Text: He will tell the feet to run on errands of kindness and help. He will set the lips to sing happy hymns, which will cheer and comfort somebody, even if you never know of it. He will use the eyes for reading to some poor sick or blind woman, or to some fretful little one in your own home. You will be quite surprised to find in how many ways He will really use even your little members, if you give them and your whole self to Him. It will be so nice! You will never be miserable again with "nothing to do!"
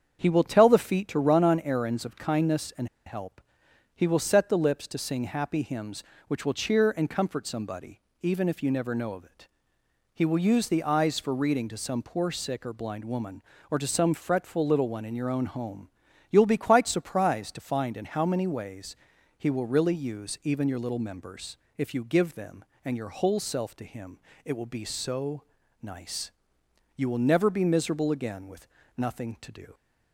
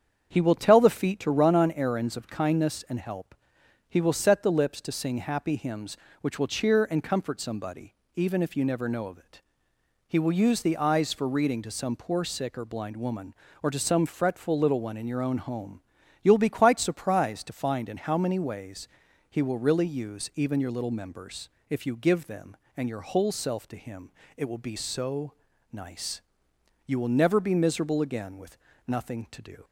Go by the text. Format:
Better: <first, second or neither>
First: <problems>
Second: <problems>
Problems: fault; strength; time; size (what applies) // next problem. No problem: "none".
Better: second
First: starts louder than the rest; strong; until 1.2 s; 7.5 dB // pauses between "and" and "help"; slight; at 2.8 s; 0.20 s long // pauses between "ways" and "He"; at 18.9 s; 0.42 s long // pauses between "so" and "nice"; at 25.4 s; 0.40 s long // pauses between "with" and "nothing"; slight; at 28.6 s; 0.28 s long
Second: starts louder than the rest; strong; until 1.3 s; 7.5 dB // pauses between "ways" and "He"; at 18.8 s; 0.42 s long // pauses between "so" and "nice"; at 25.3 s; 0.40 s long // pauses between "with" and "nothing"; slight; at 28.5 s; 0.28 s long